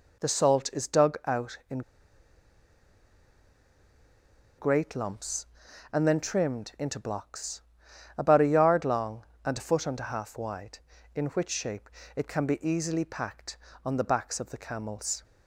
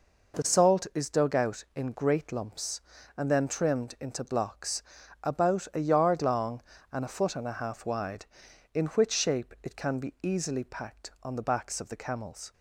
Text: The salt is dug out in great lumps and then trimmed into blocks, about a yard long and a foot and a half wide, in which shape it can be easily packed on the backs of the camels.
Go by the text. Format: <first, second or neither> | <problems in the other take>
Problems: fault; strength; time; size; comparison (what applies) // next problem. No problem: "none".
second | pauses between "in" and "great"; strong; at 1.8 s; 2.7 s long // pauses between "shape" and "it"; slight; at 11.8 s; 0.28 s long